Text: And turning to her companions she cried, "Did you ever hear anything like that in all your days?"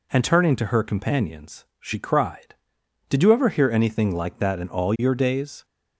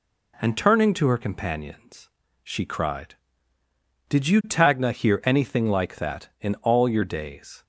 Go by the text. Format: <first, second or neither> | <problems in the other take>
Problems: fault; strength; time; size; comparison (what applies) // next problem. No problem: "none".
first | pauses between "companions" and "she"; slight; at 2.0 s; 0.34 s long // says "tagna" for "ever"; at 4.4 s